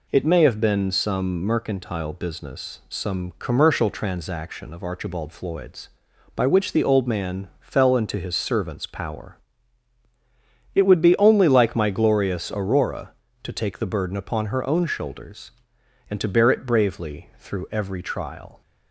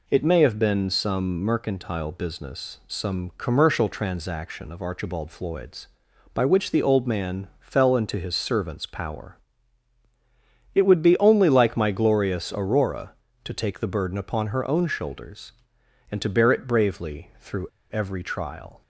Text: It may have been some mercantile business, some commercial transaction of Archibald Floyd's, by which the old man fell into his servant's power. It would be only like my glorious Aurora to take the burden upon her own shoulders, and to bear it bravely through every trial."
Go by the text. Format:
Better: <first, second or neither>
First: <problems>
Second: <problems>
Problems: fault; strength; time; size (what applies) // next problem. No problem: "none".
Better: first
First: none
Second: pauses between "through" and "every"; slight; at 17.6 s; 0.25 s long